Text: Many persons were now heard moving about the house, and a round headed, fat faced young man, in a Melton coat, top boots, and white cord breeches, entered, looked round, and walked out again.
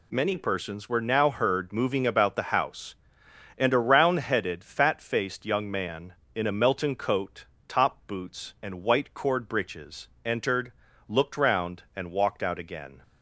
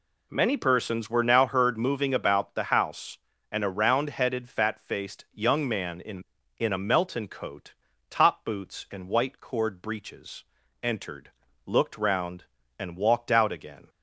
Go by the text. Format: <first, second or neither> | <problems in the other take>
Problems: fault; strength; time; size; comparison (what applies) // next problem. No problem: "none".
first | says "in" twice; at 6.5 s